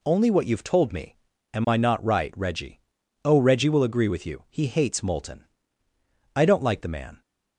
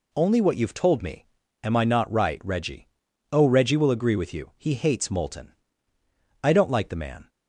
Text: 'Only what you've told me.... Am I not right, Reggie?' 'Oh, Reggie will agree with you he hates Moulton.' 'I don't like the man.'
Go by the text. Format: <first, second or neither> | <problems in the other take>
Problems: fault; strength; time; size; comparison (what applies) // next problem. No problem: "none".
neither | none